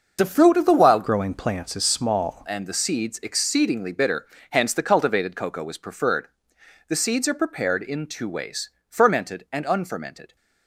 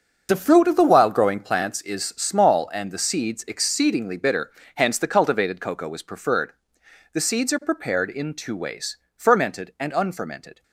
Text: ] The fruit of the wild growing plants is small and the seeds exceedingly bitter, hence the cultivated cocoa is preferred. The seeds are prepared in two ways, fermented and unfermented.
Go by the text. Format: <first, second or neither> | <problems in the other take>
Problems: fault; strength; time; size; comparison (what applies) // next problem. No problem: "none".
second | starts louder than the rest; until 1.2 s; 6 dB; also in the second // changes voice from "growing" to "small"; from 1.0 to 2.4 s; 1.4 s long